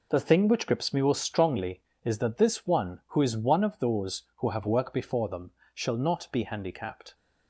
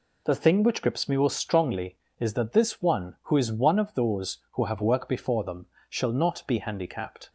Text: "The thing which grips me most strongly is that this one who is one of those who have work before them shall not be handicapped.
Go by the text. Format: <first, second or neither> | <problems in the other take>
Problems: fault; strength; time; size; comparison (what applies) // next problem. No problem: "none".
second | gets quieter; strong; throughout; 8.5 dB // pauses between "them" and "shall"; slight; at 5.5 s; 0.22 s long; slight in the second